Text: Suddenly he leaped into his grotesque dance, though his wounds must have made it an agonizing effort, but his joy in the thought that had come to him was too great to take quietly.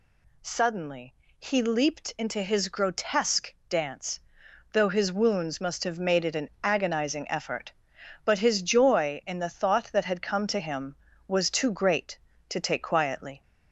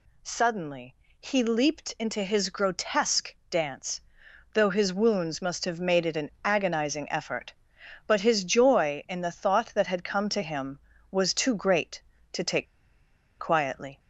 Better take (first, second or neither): first